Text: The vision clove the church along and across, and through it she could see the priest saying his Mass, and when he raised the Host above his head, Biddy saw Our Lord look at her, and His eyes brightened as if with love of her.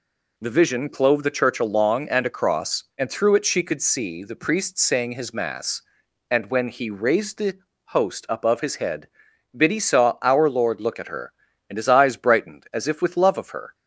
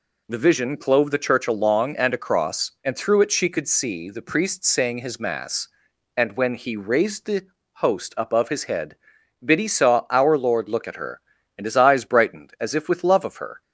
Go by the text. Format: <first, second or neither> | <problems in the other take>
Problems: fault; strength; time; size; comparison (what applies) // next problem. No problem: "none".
neither | pauses between "the" and "Host"; slight; the same in both